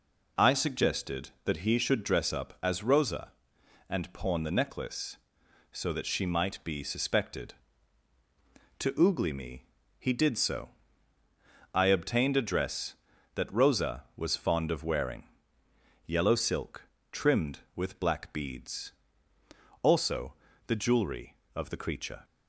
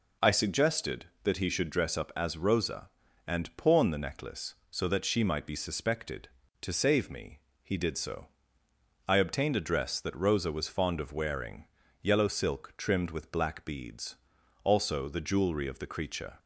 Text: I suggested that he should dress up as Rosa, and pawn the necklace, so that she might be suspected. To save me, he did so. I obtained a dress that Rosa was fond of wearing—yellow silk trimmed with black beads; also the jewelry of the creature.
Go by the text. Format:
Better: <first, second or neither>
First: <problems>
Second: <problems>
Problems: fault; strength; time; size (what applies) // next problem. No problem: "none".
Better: second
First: says "oogly" for "save"; at 9.0 s // pauses between "silk" and "trimmed"; slight; at 16.8 s; 0.30 s long // pauses between "also" and "the"; slight; at 20.3 s; 0.32 s long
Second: none